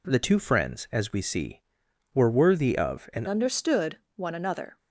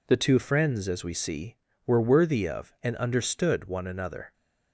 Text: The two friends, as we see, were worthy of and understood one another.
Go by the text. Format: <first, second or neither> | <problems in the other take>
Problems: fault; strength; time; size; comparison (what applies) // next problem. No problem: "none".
second | changes voice at "understood"; from 3.2 s on; 1.5 s long // pauses between "understood" and "one"; slight; at 3.9 s; 0.18 s long